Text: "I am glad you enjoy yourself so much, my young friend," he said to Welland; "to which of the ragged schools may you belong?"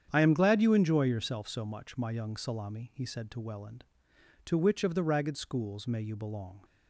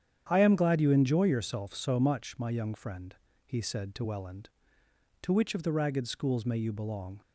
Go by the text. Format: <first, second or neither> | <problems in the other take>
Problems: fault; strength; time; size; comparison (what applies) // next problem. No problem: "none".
second | starts louder than the rest; strong; until 1.1 s; 8.5 dB; strong in the second // says "salami" for "friend"; at 2.3 s